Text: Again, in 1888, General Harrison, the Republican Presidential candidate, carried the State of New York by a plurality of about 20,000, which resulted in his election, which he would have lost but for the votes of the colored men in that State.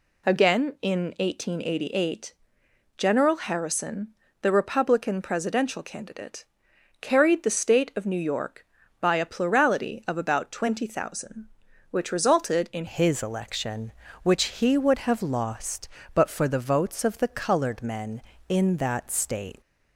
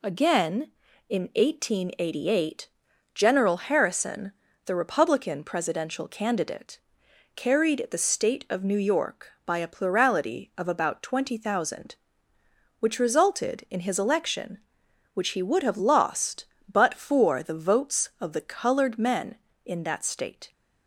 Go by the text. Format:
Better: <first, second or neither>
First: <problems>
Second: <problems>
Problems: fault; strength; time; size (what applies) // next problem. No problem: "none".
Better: second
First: changes voice at "his"; from 12.8 s on; 6.8 s long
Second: none